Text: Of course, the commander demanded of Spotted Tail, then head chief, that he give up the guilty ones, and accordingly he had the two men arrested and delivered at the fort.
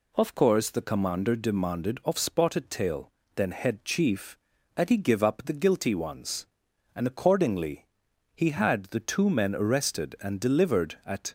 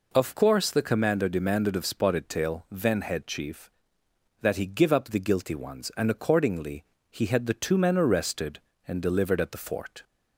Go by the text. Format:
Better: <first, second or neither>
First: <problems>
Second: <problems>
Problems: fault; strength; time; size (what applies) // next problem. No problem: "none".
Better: second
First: pauses between "accordingly" and "he"; noticeable; at 7.8 s; 0.48 s long // stops before "the fort"; at 11.2 s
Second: pauses between "accordingly" and "he"; slight; at 6.8 s; 0.26 s long